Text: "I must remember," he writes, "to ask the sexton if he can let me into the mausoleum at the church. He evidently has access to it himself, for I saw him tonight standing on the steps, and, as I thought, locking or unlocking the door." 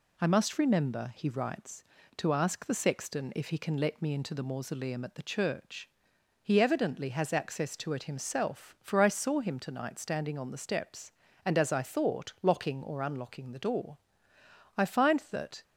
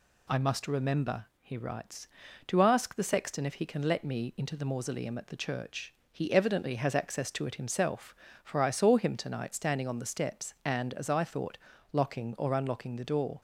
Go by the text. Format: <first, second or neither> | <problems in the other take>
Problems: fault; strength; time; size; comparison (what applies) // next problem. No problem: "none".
second | goes on to say "I find that"; noticeable; from 14.7 s on; 0.88 s long